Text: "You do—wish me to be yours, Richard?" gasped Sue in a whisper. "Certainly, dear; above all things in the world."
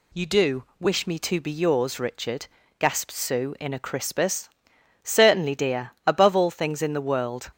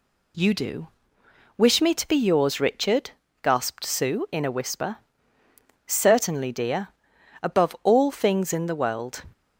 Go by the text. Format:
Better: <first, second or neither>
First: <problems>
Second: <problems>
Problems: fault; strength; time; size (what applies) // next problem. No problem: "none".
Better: second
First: says "crispus" for "whisper"; at 3.7 s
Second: none